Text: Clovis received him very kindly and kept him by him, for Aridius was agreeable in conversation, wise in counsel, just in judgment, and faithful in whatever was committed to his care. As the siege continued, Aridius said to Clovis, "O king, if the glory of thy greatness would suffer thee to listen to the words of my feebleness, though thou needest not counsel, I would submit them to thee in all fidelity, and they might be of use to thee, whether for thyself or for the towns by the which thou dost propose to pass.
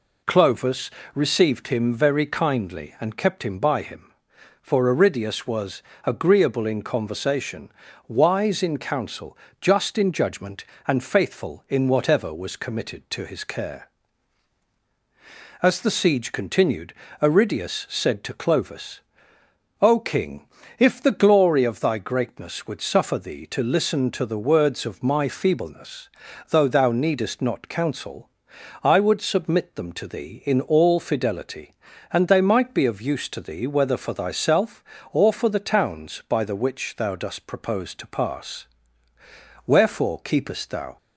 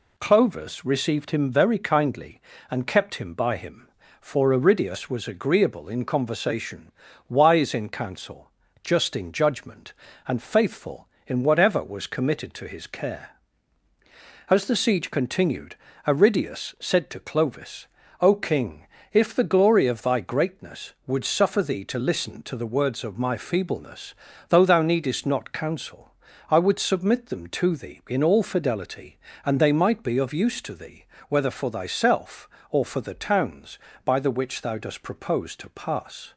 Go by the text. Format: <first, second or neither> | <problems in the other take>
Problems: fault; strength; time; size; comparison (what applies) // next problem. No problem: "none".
second | pauses between "Clovis" and "received"; slight; at 0.9 s; 0.24 s long // pauses between "was" and "agreeable"; slight; at 5.8 s; 0.24 s long // goes on to say "Wherefore keepest thou"; noticeable; from 39.6 s on; 1.3 s long